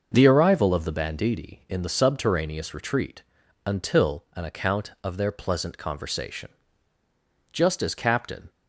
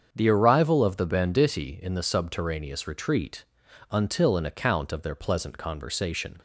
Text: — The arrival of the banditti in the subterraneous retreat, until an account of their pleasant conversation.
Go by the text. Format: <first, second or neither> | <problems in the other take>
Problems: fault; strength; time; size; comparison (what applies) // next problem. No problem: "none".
second | starts louder than the rest; noticeable; until 1.1 s; 6 dB; strong in the second // goes on to say "Just as Captain"; noticeable; from 7.5 s on; 1.0 s long